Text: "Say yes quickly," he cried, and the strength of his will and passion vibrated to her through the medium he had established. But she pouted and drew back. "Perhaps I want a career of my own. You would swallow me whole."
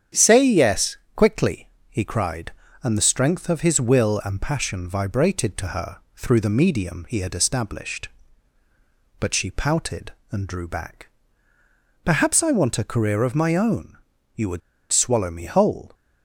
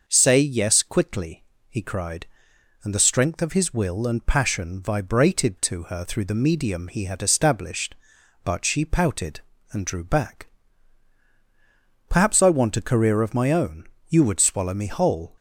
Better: second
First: starts louder than the rest; strong; until 1.3 s; 8.5 dB // pauses between "yes" and "quickly"; slight; at 0.9 s; 0.18 s long // pauses between "her" and "through"; slight; at 5.9 s; 0.18 s long // pauses between "would" and "swallow"; slight; at 14.6 s; 0.30 s long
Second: none

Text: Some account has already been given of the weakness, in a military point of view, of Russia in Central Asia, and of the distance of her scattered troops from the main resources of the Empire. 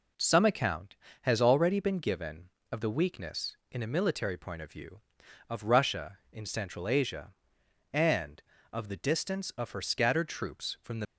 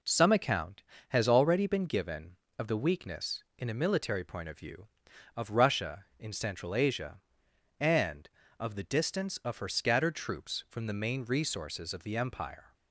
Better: second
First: stops before "main resources of the Empire"; at 11.0 s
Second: none

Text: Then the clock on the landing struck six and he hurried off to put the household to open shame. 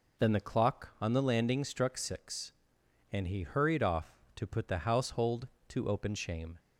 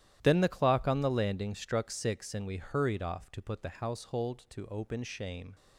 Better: first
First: none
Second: starts louder than the rest; strong; until 1.2 s; 12 dB // says "we" for "he"; at 2.4 s

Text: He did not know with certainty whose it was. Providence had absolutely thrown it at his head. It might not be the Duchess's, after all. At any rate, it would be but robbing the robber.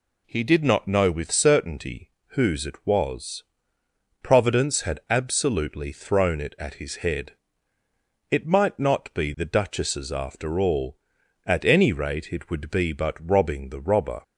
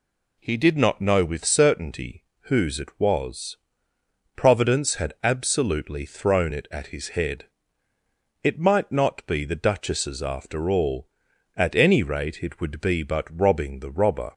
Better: neither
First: pauses between "certainty" and "whose"; slight; at 2.1 s; 0.18 s long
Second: pauses between "certainty" and "whose"; slight; at 2.2 s; 0.18 s long

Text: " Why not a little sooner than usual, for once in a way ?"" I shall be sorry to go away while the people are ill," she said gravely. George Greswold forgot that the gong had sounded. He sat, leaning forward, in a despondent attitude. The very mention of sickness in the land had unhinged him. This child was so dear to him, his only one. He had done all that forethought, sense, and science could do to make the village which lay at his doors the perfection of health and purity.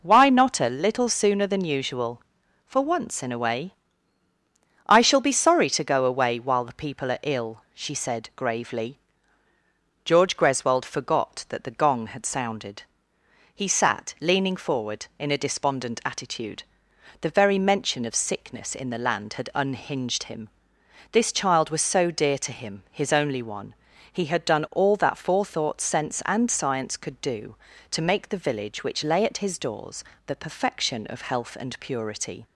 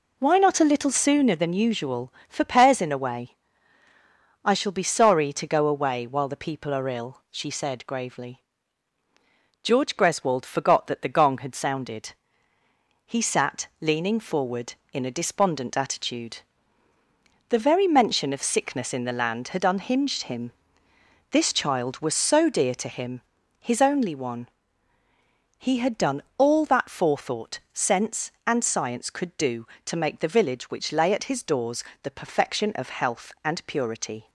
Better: first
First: pauses between "doors" and "the"; slight; at 30.0 s; 0.22 s long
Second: says "pairs" for "once"; at 2.4 s // pauses between "done" and "all"; slight; at 26.2 s; 0.16 s long // pauses between "doors" and "the"; slight; at 31.8 s; 0.20 s long

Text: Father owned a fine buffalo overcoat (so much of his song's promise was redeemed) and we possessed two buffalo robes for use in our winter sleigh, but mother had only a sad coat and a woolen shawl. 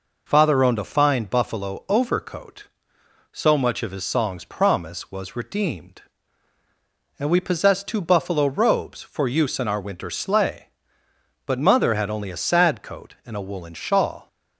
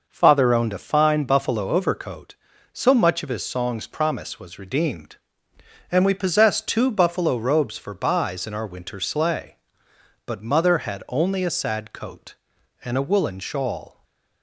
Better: first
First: none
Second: says "buys" for "use"; at 7.9 s // stays silent after the last word; slight; from 13.8 s on; 0.6 s long

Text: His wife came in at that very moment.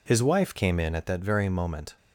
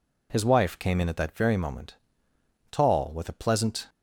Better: first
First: none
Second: goes on to say "Tall with a pleasant"; noticeable; from 2.6 s on; 1.1 s long

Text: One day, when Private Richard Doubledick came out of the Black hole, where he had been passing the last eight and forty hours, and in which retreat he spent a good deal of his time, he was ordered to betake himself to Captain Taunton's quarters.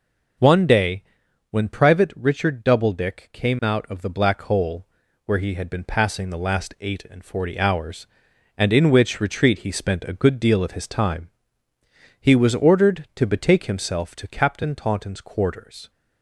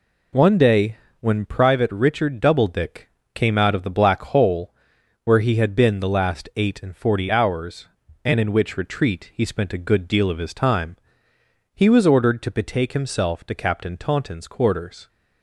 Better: first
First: none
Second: pauses between "Doubledick" and "came"; slight; at 3.0 s; 0.30 s long // skips "passing"; at 5.9 s

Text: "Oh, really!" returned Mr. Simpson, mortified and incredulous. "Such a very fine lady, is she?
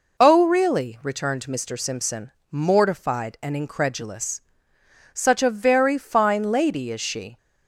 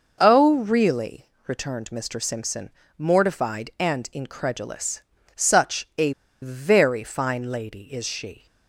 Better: first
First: none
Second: pauses between "a" and "very"; slight; at 6.1 s; 0.30 s long

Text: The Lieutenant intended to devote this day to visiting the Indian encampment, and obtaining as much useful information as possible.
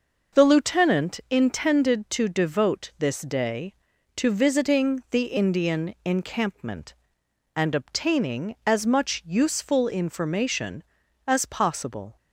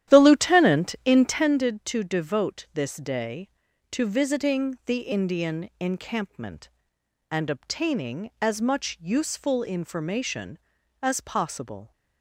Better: first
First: none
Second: starts louder than the rest; strong; until 1.6 s; 11.5 dB

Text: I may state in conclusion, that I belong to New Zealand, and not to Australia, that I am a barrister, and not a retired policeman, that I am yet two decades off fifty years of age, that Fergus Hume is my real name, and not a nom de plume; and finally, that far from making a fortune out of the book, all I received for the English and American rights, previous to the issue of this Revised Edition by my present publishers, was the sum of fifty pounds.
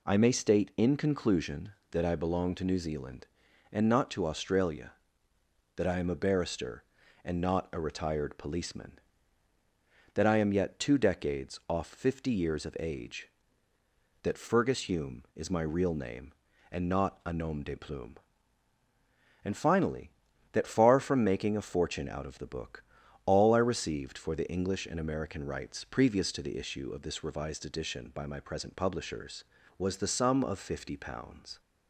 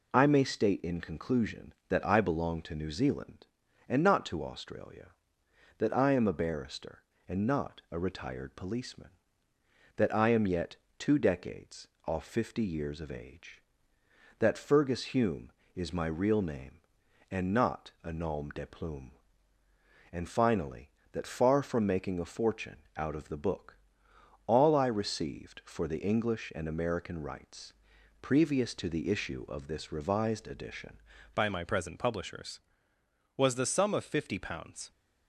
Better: first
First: none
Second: pauses between "yet" and "two"; slight; at 10.7 s; 0.20 s long // pauses between "decades" and "off"; slight; at 11.8 s; 0.20 s long // pauses between "fortune" and "out"; slight; at 22.7 s; 0.20 s long // changes voice at "by"; from 31.3 s on; 3.6 s long

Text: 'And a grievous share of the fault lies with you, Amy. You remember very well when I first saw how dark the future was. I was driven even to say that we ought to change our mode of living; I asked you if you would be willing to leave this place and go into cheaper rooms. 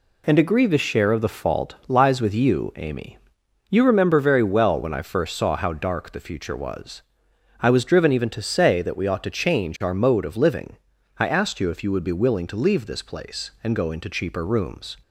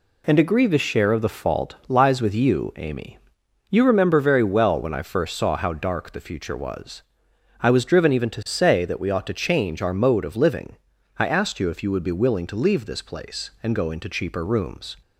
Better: neither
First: none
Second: none

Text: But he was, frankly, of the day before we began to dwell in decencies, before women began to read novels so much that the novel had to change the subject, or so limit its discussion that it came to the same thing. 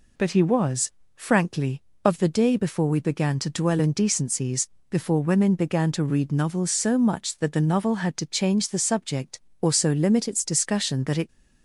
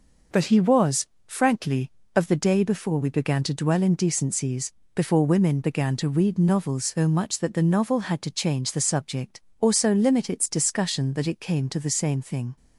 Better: second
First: stops before "came to the same thing"; at 11.2 s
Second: none

